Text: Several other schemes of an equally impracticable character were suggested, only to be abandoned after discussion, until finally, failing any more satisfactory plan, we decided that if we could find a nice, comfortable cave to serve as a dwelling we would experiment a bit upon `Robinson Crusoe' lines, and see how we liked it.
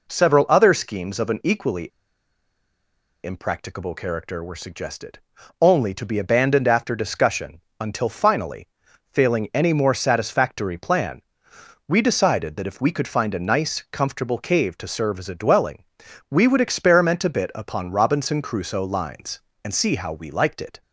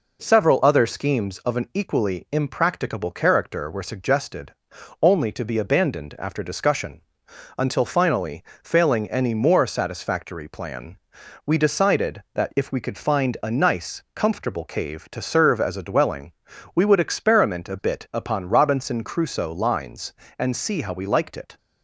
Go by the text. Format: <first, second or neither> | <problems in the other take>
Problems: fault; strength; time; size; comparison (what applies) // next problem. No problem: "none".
second | pauses between "equally" and "impracticable"; strong; at 1.8 s; 1.3 s long // pauses between "dwelling" and "we"; noticeable; at 15.8 s; 0.46 s long; also in the second